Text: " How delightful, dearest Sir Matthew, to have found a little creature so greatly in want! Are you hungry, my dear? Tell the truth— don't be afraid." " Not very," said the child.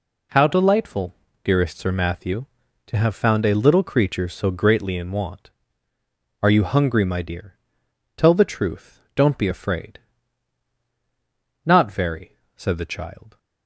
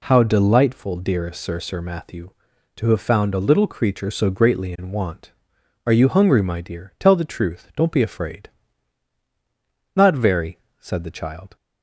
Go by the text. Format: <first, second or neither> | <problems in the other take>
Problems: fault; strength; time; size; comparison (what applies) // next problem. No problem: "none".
first | says "Sir" twice; at 1.6 s